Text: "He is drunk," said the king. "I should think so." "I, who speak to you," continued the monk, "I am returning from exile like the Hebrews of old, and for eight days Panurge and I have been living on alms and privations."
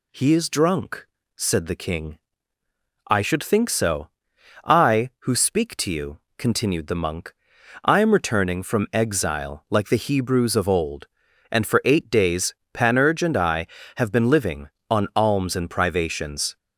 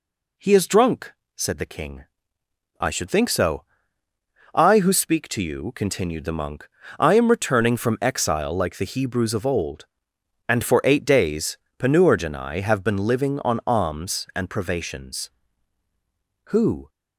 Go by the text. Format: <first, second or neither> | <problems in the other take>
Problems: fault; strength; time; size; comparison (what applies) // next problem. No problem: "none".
first | pauses between "days" and "Panurge"; slight; at 11.5 s; 0.22 s long; slight in the first // goes on to say "Who"; slight; from 16.5 s on; 0.38 s long